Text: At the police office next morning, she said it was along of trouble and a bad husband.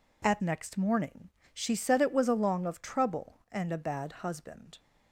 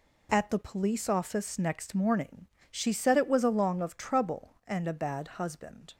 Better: second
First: skips "the police office"; at 0.4 s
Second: none

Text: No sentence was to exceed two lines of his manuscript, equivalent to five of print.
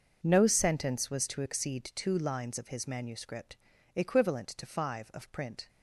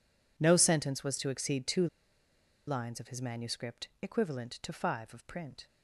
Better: first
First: none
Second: pauses between "two" and "lines"; noticeable; at 1.8 s; 0.80 s long

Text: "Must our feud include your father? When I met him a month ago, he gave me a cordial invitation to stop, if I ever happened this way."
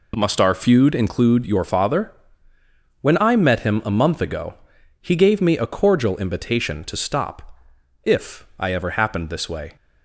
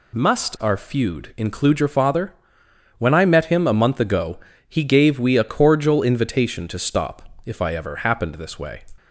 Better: first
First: none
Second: says "we" for "me"; at 5.2 s

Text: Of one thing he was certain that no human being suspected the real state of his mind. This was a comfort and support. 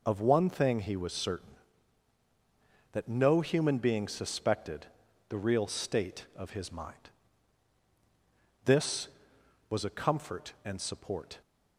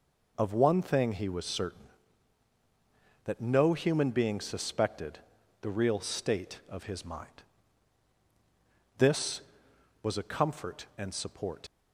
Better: first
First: pauses between "suspected" and "the"; at 4.8 s; 0.42 s long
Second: pauses between "suspected" and "the"; at 5.1 s; 0.42 s long // leaves "support" unfinished; at 11.6 s; 70 ms

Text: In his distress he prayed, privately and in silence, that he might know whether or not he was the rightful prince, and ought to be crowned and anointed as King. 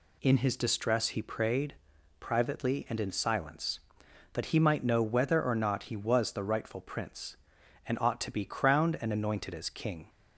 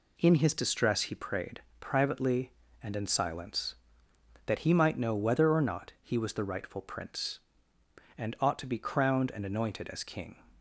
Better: neither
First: none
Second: none

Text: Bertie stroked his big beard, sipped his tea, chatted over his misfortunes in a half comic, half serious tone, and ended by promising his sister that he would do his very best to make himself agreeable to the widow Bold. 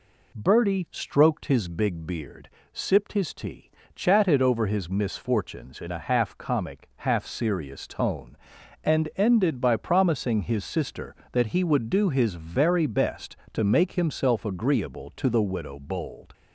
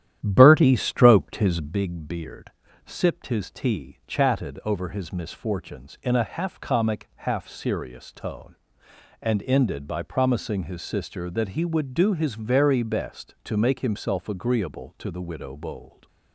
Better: first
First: none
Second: starts louder than the rest; strong; until 1.9 s; 11 dB

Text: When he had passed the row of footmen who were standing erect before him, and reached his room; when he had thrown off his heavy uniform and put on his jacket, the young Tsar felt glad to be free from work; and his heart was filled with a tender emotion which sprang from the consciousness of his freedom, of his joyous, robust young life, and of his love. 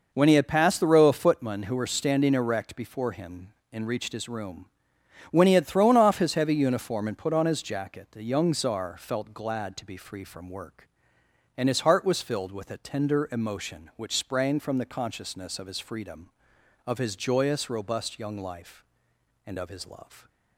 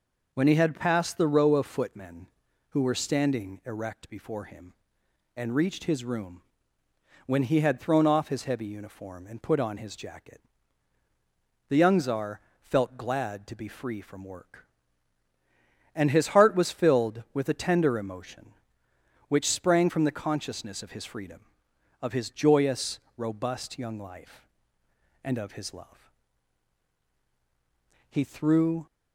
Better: first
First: none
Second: pauses between "Tsar" and "felt"; slight; at 12.3 s; 0.22 s long // goes on to say "He threw"; noticeable; from 28.0 s on; 0.78 s long

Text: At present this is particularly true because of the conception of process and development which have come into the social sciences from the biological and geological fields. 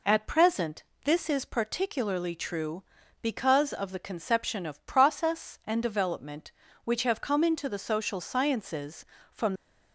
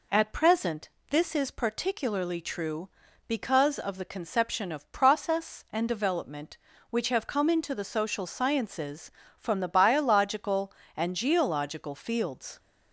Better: second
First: pauses between "present" and "this"; slight; at 0.8 s; 0.22 s long // stops before "the biological and geological fields"; at 9.5 s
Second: pauses between "present" and "this"; slight; at 0.8 s; 0.22 s long

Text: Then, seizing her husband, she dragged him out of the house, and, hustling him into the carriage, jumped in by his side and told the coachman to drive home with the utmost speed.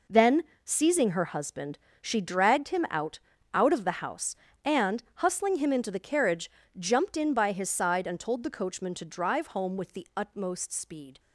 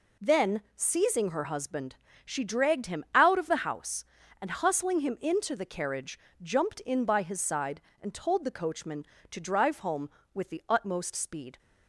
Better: second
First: says "out" twice; at 3.5 s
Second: none

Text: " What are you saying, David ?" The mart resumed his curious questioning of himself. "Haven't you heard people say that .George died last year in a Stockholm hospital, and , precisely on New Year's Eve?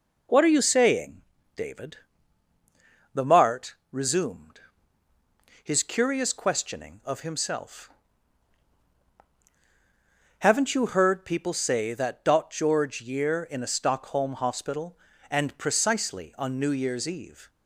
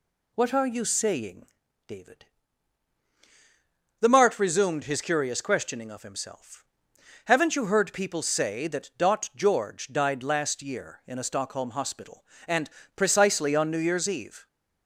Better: second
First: pauses between "mart" and "resumed"; slight; at 3.7 s; 0.17 s long // pauses between "resumed" and "his"; at 4.5 s; 1.0 s long // skips "died last"; at 13.0 s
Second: none

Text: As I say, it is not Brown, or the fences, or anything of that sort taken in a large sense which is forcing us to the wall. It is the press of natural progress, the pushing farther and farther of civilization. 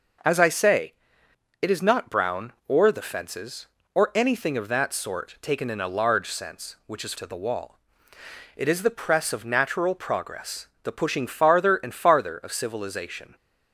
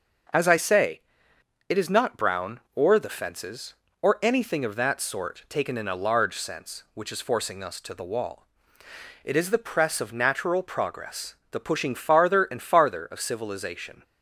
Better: second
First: starts louder than the rest; noticeable; until 1.9 s; 6 dB // skips "forcing us"; at 7.1 s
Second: starts louder than the rest; until 2.0 s; 6.5 dB

